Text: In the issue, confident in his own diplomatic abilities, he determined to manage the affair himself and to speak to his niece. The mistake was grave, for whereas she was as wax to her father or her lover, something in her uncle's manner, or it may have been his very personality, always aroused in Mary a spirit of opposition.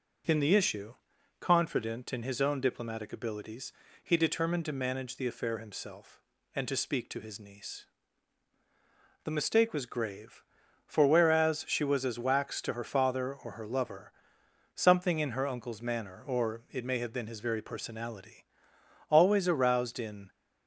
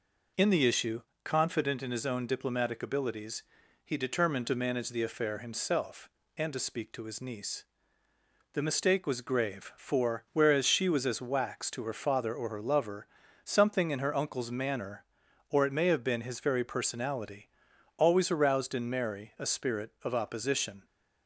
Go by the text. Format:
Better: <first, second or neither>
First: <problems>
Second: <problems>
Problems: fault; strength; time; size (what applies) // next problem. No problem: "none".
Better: second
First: stops before "Mary a spirit of opposition"; at 20.2 s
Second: none